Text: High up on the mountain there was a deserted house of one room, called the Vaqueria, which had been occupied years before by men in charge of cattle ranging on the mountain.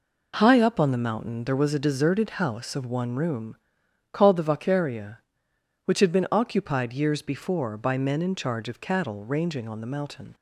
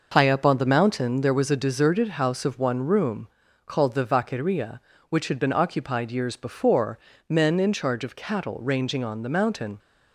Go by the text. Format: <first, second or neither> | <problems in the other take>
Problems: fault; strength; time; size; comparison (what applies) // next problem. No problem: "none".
first | skips "by"; at 7.1 s